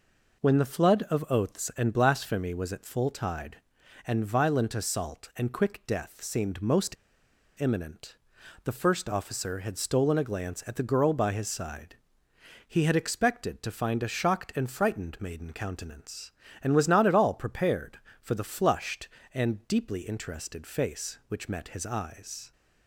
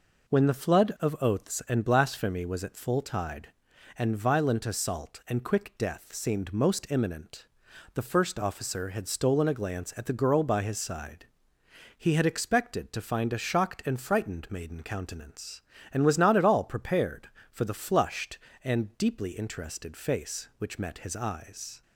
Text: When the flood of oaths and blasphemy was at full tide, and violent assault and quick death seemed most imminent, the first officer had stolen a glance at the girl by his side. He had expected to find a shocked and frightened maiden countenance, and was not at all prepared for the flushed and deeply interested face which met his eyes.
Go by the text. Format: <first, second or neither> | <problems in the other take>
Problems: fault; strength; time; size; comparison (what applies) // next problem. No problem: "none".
second | pauses between "most" and "imminent"; noticeable; at 6.9 s; 0.63 s long